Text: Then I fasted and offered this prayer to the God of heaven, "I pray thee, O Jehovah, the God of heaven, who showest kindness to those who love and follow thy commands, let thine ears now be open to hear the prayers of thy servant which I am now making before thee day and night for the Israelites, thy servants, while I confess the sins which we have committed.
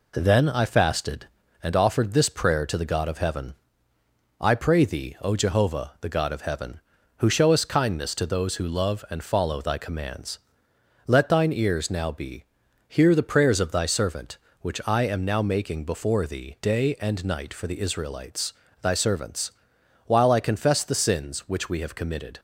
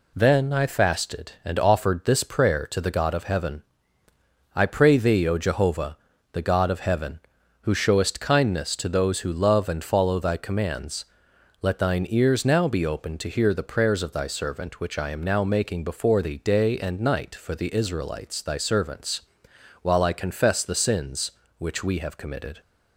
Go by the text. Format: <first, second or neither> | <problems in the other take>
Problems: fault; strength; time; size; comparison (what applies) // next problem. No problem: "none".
second | skips "open to"; at 12.6 s